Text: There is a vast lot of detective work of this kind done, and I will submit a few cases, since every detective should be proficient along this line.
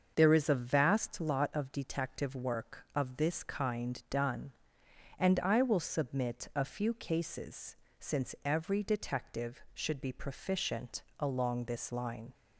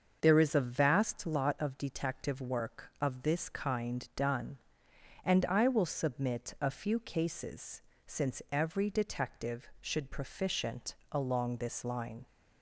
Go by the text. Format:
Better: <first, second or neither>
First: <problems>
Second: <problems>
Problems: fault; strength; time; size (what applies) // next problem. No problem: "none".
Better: first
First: starts louder than the rest; until 1.1 s; 6.5 dB // pauses between "proficient" and "along"; slight; at 11.0 s; 0.16 s long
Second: starts louder than the rest; until 1.2 s; 6.5 dB // skips "be"; at 10.0 s // pauses between "proficient" and "along"; slight; at 10.9 s; 0.16 s long